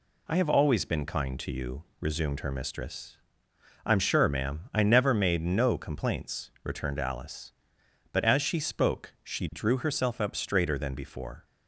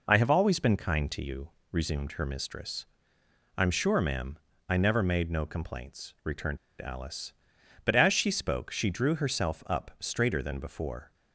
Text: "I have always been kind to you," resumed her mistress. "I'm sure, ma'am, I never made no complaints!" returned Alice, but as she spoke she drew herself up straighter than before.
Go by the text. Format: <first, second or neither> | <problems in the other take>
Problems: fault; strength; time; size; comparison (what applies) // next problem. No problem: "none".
first | pauses between "returned" and "Alice"; slight; at 6.5 s; 0.23 s long